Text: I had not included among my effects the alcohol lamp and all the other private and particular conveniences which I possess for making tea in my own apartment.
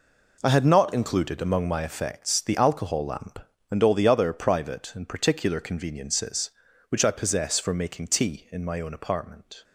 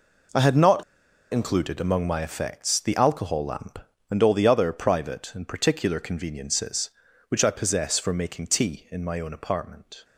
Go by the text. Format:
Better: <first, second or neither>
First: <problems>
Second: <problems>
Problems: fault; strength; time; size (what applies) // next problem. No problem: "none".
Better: first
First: none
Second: pauses between "not" and "included"; noticeable; at 0.8 s; 0.48 s long